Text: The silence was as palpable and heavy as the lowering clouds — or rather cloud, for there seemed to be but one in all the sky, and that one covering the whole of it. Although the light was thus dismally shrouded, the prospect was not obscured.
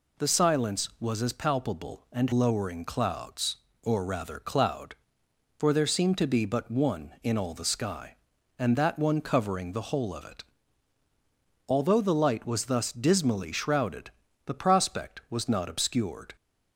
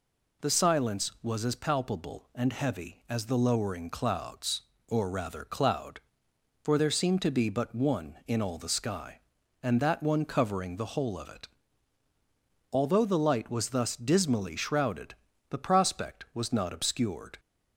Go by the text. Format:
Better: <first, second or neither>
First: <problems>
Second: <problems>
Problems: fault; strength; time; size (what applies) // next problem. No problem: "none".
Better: second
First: skips "heavy as the"; at 2.3 s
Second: none